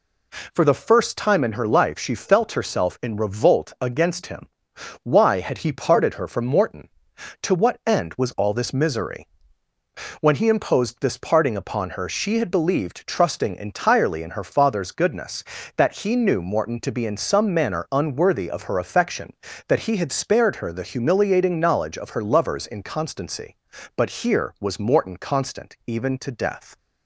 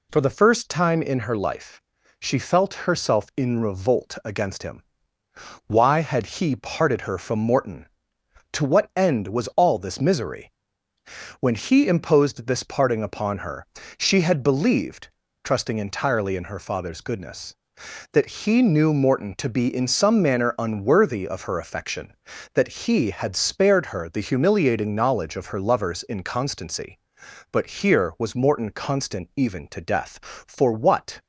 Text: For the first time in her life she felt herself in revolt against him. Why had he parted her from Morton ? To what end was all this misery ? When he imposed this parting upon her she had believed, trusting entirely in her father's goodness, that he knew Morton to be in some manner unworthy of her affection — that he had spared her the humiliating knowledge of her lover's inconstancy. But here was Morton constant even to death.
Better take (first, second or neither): first